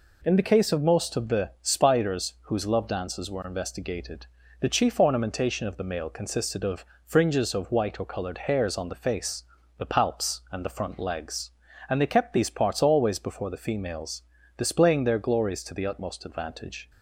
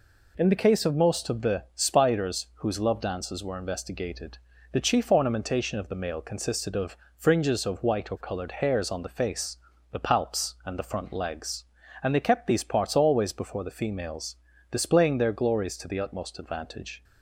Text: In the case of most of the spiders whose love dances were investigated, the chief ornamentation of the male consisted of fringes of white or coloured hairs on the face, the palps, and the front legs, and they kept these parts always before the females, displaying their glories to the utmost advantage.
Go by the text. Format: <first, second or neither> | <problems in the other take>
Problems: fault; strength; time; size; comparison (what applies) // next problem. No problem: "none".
neither | pauses between "of" and "fringes"; slight; the same in both